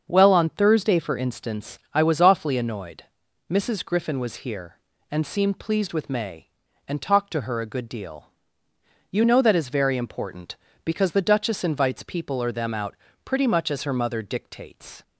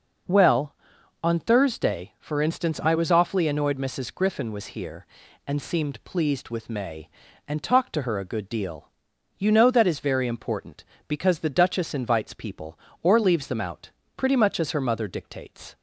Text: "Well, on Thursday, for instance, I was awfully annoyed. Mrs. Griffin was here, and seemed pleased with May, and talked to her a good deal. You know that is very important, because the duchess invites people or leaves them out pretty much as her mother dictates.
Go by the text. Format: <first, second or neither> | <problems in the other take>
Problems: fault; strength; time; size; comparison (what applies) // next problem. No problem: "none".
second | starts louder than the rest; until 1.1 s; 7 dB // skips "leaves"; at 12.5 s // pauses between "out" and "pretty"; slight; at 12.9 s; 0.30 s long; slight in the second